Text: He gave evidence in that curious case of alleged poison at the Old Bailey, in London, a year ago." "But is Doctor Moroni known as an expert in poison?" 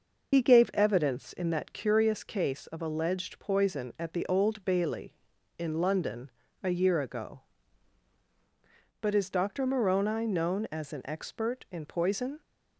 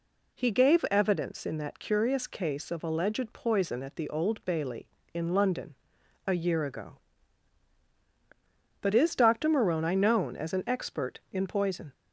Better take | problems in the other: second | loses the start of "He"; at 0.3 s; 60 ms

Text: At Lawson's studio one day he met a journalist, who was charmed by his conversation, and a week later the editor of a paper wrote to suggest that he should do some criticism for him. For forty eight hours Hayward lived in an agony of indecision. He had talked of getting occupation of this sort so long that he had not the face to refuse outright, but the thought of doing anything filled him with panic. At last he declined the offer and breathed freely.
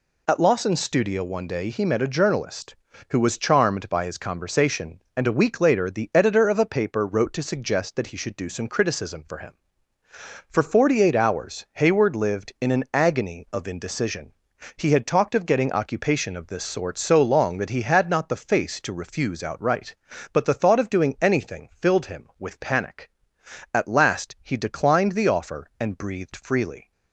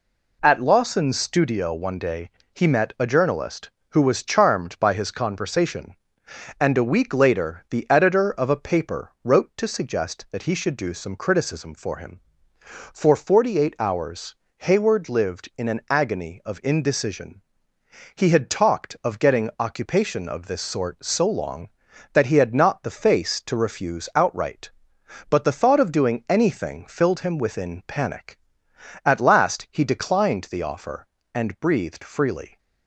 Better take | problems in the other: first | pauses between "day" and "he"; slight; at 2.2 s; 0.24 s long // pauses between "hours" and "Hayward"; slight; at 14.3 s; 0.24 s long // says "within" for "with"; at 27.3 s

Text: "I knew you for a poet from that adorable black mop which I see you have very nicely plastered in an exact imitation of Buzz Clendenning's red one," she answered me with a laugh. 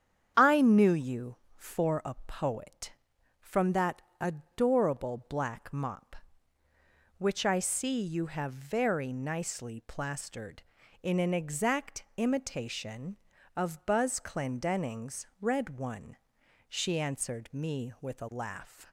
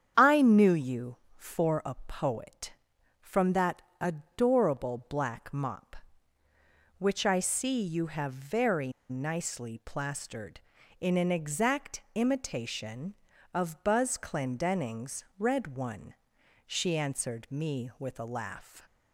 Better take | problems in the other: first | starts louder than the rest; strong; until 1.3 s; 8.5 dB; strong in the first // pauses between "that" and "adorable"; slight; at 3.8 s; 0.18 s long; slight in the first // pauses between "very" and "nicely"; slight; at 8.9 s; 0.18 s long // pauses between "Clendenning's" and "red"; slight; at 15.2 s; 0.16 s long; slight in the first

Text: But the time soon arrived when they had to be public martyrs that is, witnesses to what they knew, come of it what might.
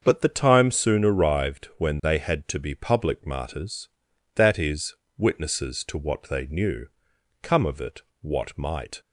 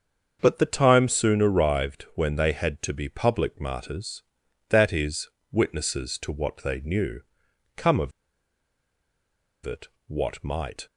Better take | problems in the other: first | starts louder than the rest; until 1.4 s; 7 dB; also in the first // pauses between "of" and "it"; strong; at 8.1 s; 1.5 s long // pauses between "it" and "what"; slight; at 9.8 s; 0.18 s long; slight in the first

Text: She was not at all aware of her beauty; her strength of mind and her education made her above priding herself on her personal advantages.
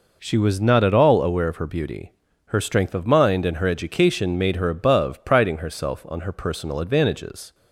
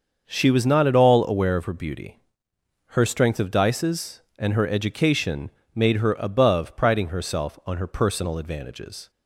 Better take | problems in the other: first | starts louder than the rest; until 1.2 s; 6.5 dB // says "dices" for "mind"; at 3.5 s // pauses between "education" and "made"; slight; at 5.5 s; 0.24 s long

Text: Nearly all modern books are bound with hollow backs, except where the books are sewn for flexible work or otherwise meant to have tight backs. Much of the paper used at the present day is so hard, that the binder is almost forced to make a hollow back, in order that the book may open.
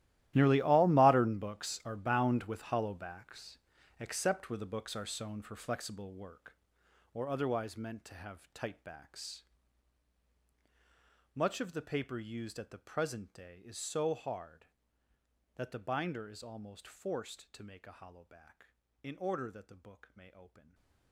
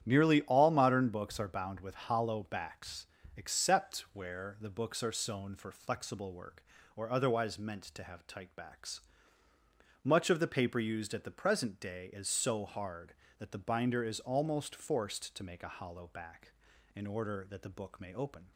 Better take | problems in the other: second | gets quieter; strong; throughout; 17.5 dB // starts louder than the rest; strong; until 1.3 s; 14.5 dB; strong in the second // stays silent after the last word; slight; from 20.5 s on; 0.6 s long

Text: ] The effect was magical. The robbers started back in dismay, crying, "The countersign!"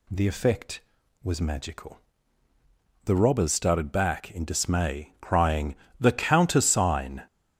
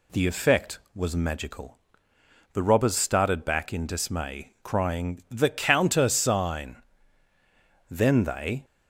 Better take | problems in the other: first | goes on to say "Then they"; noticeable; from 7.8 s on; 0.76 s long

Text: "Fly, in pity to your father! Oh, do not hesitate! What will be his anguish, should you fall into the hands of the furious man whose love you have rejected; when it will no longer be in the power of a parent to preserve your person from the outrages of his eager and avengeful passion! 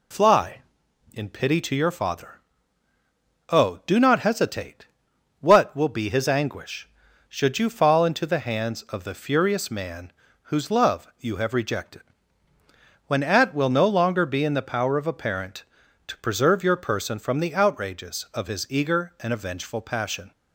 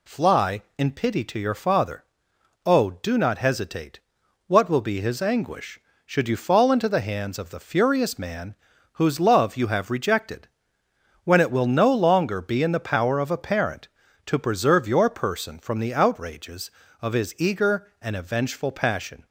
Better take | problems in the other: second | pauses between "man" and "whose"; at 10.1 s; 0.40 s long; also in the second // says "at" for "it"; at 13.2 s

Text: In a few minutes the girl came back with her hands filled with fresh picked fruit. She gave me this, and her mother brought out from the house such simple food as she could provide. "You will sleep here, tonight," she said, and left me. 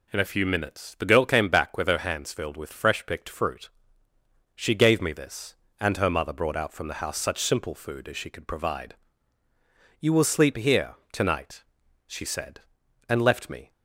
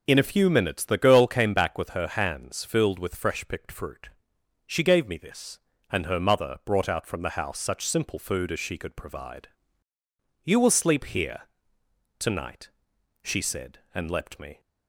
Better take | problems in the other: first | says "leapt" for "left"; at 14.0 s

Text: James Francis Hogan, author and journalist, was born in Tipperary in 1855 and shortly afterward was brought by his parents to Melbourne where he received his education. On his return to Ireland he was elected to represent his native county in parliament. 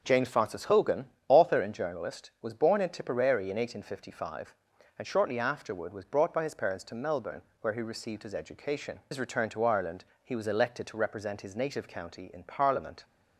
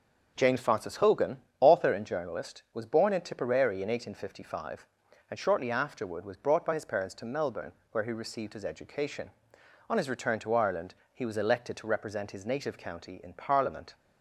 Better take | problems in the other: second | pauses between "Melbourne" and "where"; slight; at 7.4 s; 0.18 s long; slight in the second // skips "On"; at 9.0 s // pauses between "Ireland" and "he"; slight; at 10.0 s; 0.18 s long; slight in the second

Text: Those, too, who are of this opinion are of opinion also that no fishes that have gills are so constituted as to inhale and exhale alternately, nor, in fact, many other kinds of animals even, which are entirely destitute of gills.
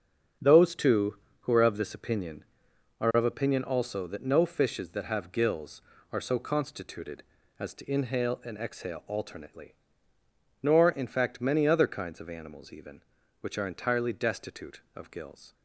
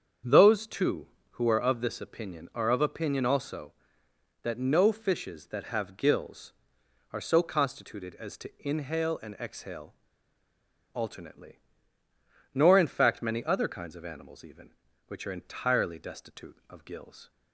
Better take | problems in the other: first | starts louder than the rest; strong; until 1.5 s; 7.5 dB; also in the first // pauses between "exhale" and "alternately"; at 9.9 s; 1.0 s long

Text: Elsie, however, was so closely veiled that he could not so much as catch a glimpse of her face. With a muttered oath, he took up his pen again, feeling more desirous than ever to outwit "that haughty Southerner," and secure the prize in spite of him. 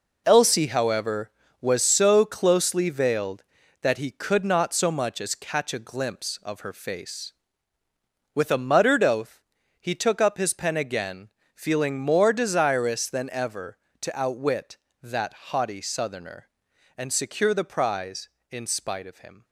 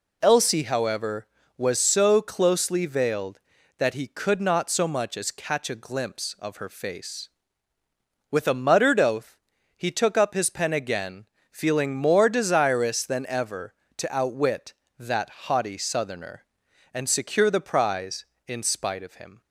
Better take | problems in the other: second | gets quieter; strong; throughout; 9.5 dB // pauses between "that" and "haughty"; slight; at 15.3 s; 0.18 s long; slight in the second

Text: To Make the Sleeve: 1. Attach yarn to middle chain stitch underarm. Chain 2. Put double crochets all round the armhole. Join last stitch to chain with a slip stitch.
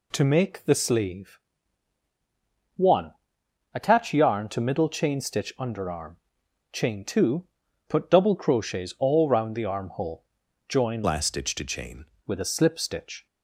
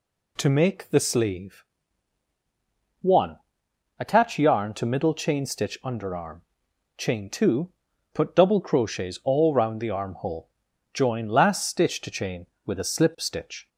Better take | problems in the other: second | changes voice from "last" to "chain"; from 11.0 to 12.0 s; 1.0 s long

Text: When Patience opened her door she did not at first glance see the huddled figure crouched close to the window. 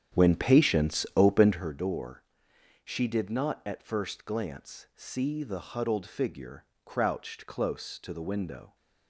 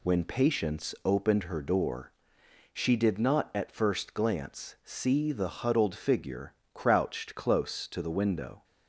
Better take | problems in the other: second | starts louder than the rest; strong; until 1.8 s; 9 dB // pauses between "door" and "she"; noticeable; at 2.2 s; 0.62 s long; noticeable in the second // pauses between "figure" and "crouched"; slight; at 6.6 s; 0.20 s long; slight in the second

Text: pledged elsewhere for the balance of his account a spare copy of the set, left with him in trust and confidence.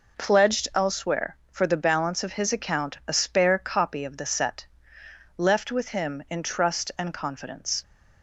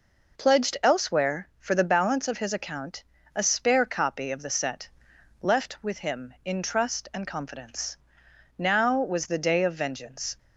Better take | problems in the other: first | pauses between "account" and "a"; slight; at 3.0 s; 0.32 s long // goes on to say "Now was the day of vengeance"; strong; from 8.5 s on; 1.8 s long

